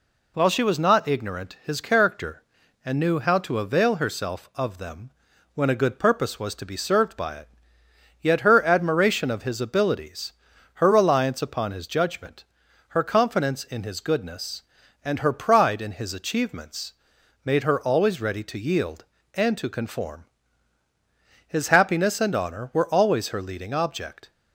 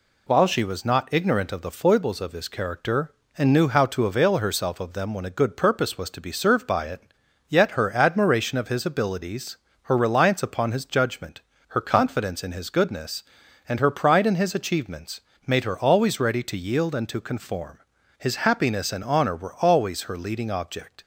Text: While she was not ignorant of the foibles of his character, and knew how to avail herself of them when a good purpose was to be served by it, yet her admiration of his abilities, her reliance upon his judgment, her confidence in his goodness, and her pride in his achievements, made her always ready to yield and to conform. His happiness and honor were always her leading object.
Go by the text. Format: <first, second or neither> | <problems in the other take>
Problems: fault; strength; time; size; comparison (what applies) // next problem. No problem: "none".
second | skips "of the foibles of"; at 1.6 s // pauses between "them" and "when"; at 5.0 s; 0.44 s long